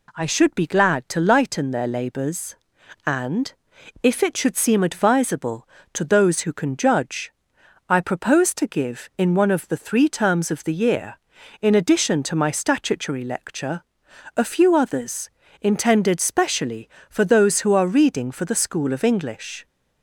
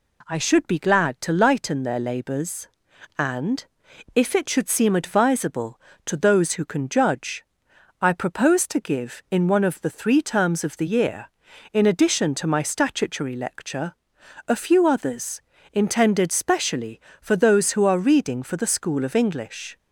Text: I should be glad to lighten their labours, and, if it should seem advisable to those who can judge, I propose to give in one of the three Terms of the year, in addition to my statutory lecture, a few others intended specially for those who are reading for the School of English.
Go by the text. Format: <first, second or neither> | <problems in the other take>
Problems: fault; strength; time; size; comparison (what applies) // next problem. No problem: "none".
neither | pauses between "others" and "intended"; slight; the same in both